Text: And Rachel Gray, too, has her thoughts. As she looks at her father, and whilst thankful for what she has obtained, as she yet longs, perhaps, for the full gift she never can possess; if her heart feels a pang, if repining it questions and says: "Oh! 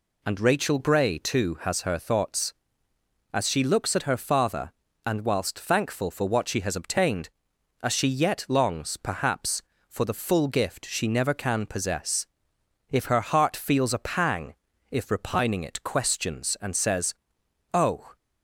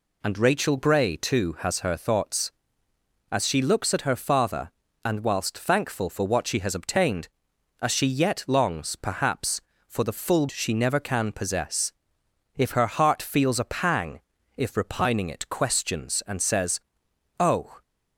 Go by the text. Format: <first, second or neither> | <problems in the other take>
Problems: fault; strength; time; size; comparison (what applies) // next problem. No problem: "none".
first | skips "gift"; at 10.4 s